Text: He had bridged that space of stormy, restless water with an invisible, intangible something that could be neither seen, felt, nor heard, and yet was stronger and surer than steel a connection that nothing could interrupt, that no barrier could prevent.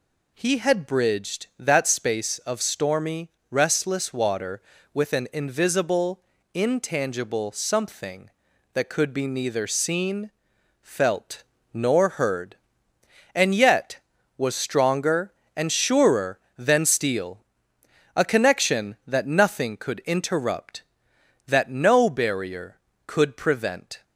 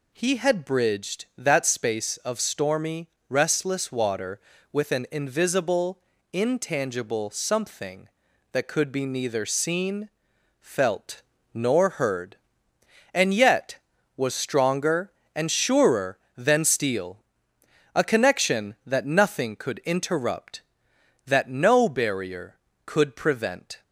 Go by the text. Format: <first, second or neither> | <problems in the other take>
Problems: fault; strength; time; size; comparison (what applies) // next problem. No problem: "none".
neither | pauses between "steel" and "a"; noticeable; the same in both